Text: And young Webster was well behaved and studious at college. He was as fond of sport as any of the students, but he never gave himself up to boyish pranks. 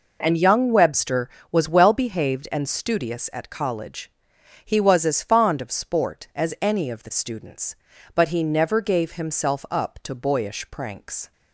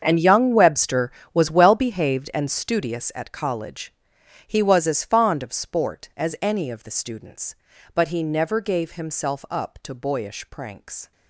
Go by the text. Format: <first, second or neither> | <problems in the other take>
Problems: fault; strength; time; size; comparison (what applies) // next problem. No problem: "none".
first | gets quieter; strong; throughout; 15.5 dB